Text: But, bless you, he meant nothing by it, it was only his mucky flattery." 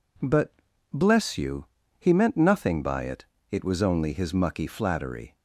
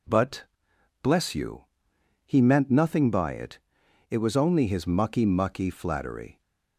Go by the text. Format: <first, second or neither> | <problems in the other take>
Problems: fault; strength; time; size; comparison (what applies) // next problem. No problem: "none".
first | says "mucky" twice; at 5.2 s